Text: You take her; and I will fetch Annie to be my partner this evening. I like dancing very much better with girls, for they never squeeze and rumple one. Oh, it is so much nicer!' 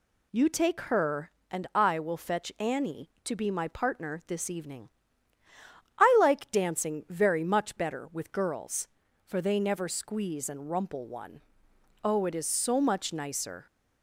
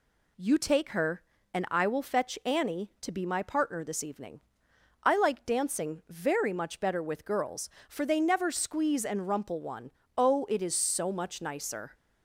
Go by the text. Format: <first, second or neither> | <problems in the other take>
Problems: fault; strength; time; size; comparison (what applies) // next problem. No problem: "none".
neither | none